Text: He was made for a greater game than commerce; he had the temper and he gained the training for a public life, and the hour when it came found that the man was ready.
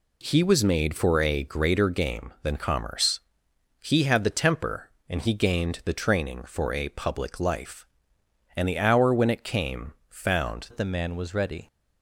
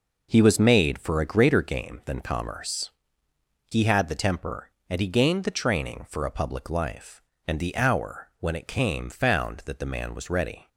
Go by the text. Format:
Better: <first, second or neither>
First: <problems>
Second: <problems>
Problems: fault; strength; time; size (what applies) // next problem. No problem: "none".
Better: second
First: pauses between "came" and "found"; slight; at 9.9 s; 0.16 s long // changes voice at "that"; from 10.6 s on; 1.0 s long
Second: none